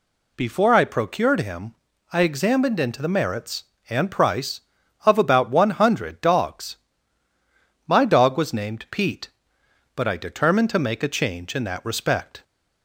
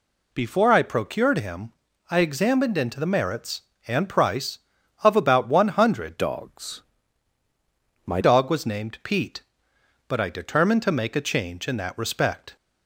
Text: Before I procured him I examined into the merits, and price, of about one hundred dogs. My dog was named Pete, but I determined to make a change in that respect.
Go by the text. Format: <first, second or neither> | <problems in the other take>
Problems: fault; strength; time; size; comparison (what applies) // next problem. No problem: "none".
first | pauses between "him" and "I"; at 1.7 s; 0.38 s long; also in the first // changes voice from "dogs" to "My"; from 6.1 to 8.2 s; 2.1 s long